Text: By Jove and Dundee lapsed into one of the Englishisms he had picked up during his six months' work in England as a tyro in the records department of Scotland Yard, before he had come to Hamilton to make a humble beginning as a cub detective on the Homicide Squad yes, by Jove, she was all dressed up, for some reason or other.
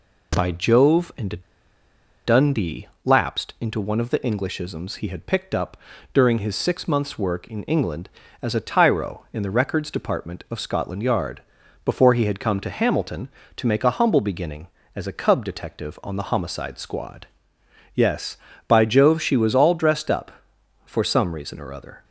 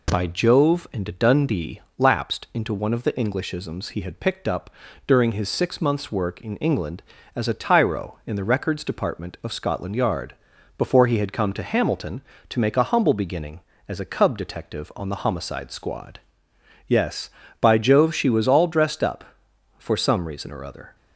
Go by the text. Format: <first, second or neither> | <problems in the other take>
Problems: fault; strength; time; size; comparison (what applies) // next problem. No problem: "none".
second | pauses between "and" and "Dundee"; noticeable; at 1.3 s; 0.86 s long // pauses between "Dundee" and "lapsed"; slight; at 2.8 s; 0.18 s long; slight in the second // pauses between "up" and "during"; slight; at 5.7 s; 0.34 s long; slight in the second // pauses between "Squad" and "yes"; noticeable; at 17.2 s; 0.66 s long; noticeable in the second